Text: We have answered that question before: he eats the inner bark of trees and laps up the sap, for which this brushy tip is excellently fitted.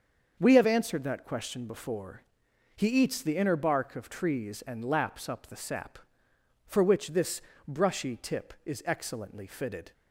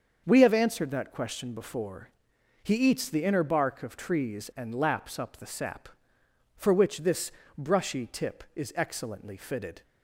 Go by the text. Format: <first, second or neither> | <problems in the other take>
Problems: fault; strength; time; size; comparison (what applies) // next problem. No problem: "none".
neither | starts louder than the rest; the same in both // pauses between "this" and "brushy"; slight; the same in both